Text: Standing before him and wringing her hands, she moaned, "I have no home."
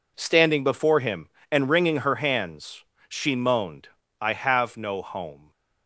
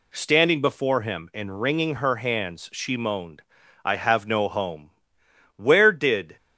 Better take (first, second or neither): first